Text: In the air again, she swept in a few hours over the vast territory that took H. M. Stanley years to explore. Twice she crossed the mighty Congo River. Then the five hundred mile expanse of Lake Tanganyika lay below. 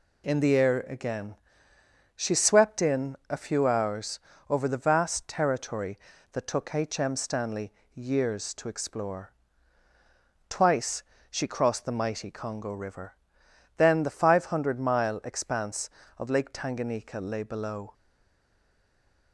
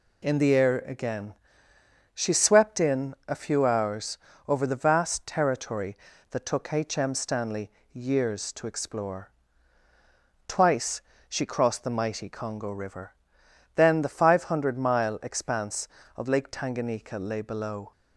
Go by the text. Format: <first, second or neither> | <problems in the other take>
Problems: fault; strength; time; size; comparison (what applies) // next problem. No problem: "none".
second | pauses between "hours" and "over"; slight; at 4.1 s; 0.30 s long; slight in the second // pauses between "Stanley" and "years"; slight; at 7.7 s; 0.22 s long; slight in the second // pauses between "Twice" and "she"; slight; at 11.0 s; 0.26 s long; slight in the second // stays silent after the last word; noticeable; from 17.9 s on; 1.4 s long